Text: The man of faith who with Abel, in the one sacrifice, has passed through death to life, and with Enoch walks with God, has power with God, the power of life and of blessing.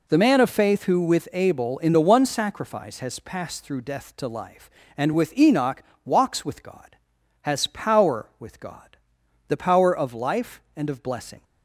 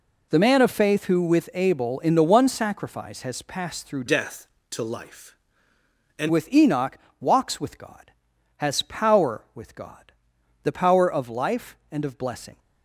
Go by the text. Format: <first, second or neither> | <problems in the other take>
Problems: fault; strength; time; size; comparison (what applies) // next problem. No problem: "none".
first | changes voice from "death" to "and"; from 4.0 to 6.2 s; 2.2 s long // pauses between "Enoch" and "walks"; slight; at 6.9 s; 0.22 s long; slight in the first